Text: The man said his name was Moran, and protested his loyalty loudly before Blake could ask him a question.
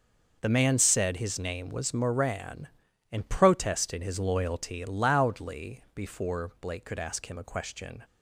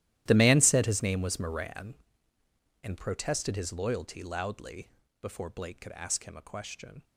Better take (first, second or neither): first